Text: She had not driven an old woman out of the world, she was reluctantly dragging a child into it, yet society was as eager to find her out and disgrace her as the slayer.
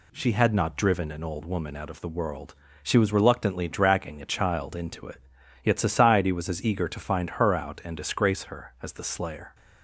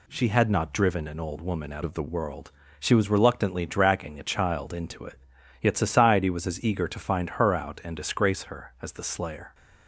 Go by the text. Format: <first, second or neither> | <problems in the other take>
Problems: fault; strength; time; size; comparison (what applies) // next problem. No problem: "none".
first | changes voice from "of" to "the"; from 1.8 to 2.0 s; 0.2 s long